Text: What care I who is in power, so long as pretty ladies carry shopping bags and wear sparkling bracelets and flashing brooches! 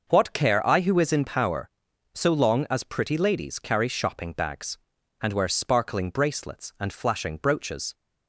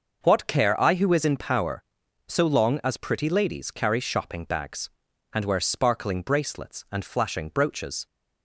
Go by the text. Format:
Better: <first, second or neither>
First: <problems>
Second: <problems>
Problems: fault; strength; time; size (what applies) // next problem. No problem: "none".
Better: neither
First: starts louder than the rest; noticeable; until 1.1 s; 6 dB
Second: starts louder than the rest; noticeable; until 1.2 s; 6 dB